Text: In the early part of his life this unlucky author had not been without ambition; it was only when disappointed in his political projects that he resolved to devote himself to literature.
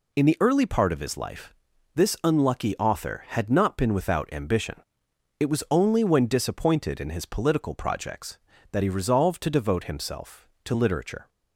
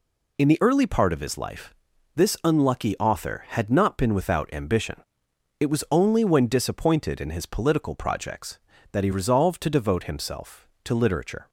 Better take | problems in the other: neither | pauses between "life" and "this"; the same in both

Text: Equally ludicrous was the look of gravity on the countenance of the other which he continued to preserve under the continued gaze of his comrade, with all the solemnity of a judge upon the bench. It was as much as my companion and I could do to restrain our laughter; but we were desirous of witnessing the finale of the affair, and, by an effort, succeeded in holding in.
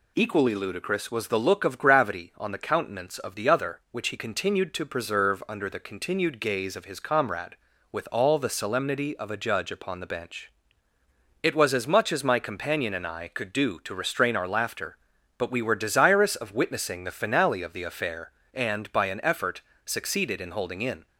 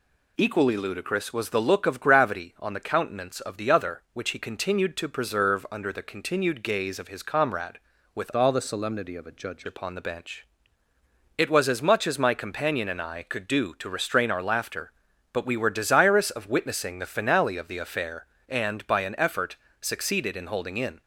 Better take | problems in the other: first | changes voice from "all" to "judge"; from 8.3 to 9.6 s; 1.3 s long

